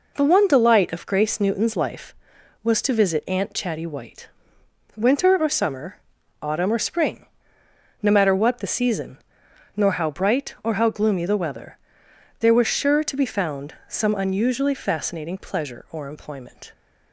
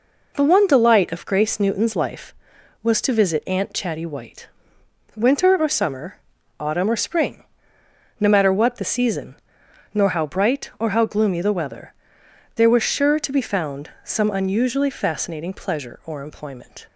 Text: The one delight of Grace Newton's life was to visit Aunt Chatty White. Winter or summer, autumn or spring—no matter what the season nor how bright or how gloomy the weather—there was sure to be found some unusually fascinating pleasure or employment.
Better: neither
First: pauses between "season" and "nor"; noticeable; at 9.1 s; 0.56 s long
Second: pauses between "season" and "nor"; noticeable; at 9.3 s; 0.56 s long

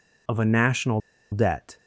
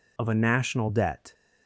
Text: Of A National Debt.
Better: second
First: pauses between "National" and "Debt"; slight; at 1.0 s; 0.32 s long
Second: none

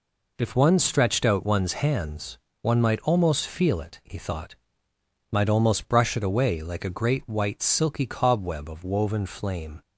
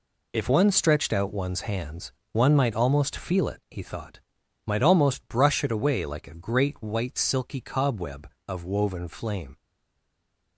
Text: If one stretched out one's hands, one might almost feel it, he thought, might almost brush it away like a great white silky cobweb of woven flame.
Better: first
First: none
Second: stays silent after the last word; from 9.5 s on; 1.0 s long

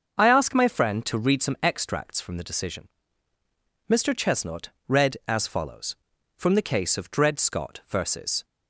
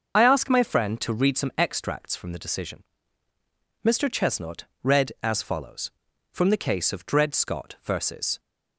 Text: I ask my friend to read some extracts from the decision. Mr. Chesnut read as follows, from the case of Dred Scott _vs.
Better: first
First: starts louder than the rest; until 1.1 s; 6.5 dB // pauses between "Chesnut" and "read"; slight; at 4.6 s; 0.18 s long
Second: loses the start of "I"; at 0.1 s; 55 ms // starts louder than the rest; until 1.2 s; 6.5 dB // pauses between "Chesnut" and "read"; slight; at 4.6 s; 0.18 s long

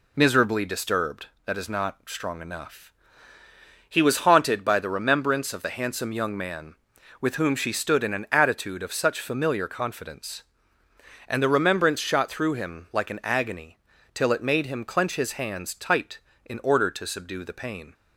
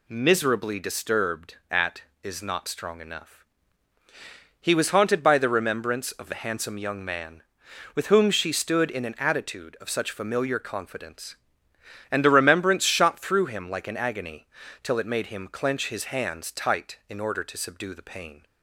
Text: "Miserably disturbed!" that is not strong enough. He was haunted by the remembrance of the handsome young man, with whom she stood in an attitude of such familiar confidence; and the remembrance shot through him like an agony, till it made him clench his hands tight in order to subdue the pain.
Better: first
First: none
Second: says "at" for "that"; at 1.7 s

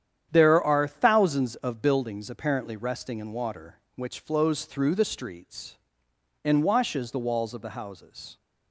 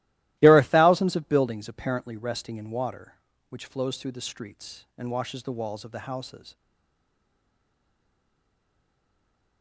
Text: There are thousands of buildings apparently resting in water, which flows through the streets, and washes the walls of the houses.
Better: first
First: starts louder than the rest; strong; until 1.3 s; 9.5 dB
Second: starts louder than the rest; strong; until 1.4 s; 16.5 dB // stays silent after the last word; strong; from 6.5 s on; 3.1 s long

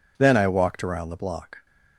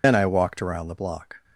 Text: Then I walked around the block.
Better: first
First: none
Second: loses the start of "Then"; at 0.0 s; 85 ms

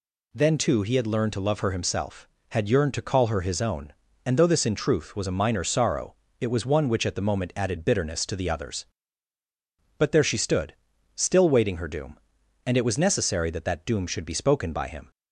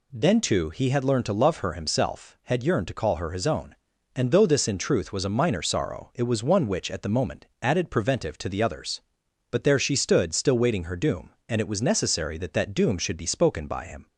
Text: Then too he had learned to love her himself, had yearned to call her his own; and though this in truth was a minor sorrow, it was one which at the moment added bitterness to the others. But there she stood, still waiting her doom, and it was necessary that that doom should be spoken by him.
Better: first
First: none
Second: pauses between "moment" and "added"; slight; at 7.4 s; 0.16 s long // says "preventive" for "bitterness"; at 7.9 s

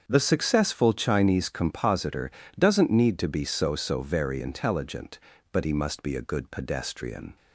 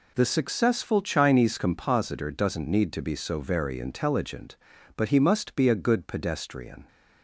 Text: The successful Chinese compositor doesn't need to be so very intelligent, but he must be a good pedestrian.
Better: second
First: starts louder than the rest; until 1.0 s; 7 dB // pauses between "compositor" and "doesn't"; slight; at 2.2 s; 0.26 s long // says "so" twice; at 3.7 s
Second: none

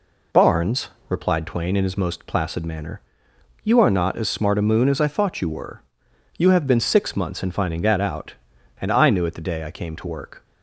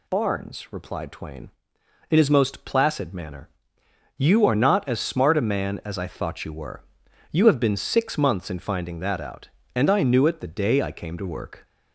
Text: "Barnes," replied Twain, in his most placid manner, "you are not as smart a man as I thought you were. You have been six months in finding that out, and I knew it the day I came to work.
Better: second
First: says "moon" for "man"; at 4.6 s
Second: none

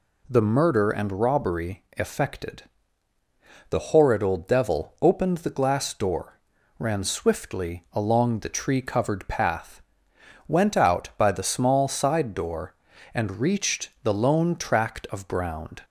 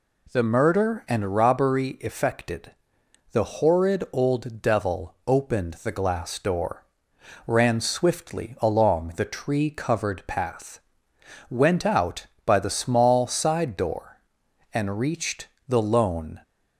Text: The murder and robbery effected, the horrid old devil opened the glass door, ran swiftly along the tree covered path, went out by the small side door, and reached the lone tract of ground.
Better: first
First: none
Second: pauses between "reached" and "the"; slight; at 15.4 s; 0.18 s long // stops before "tract of ground"; at 16.4 s

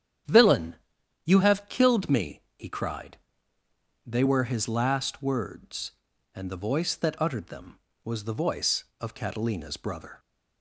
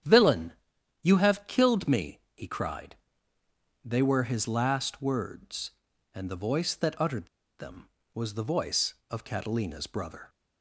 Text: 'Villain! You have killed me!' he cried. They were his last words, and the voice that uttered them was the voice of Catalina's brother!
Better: first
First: starts louder than the rest; strong; until 1.7 s; 9 dB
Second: starts louder than the rest; strong; until 1.5 s; 9 dB // pauses between "uttered" and "them"; slight; at 7.2 s; 0.32 s long

